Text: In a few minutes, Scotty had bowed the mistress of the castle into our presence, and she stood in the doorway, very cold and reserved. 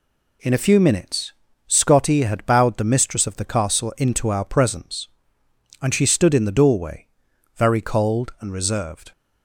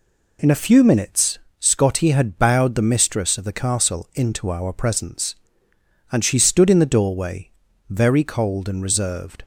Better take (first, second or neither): neither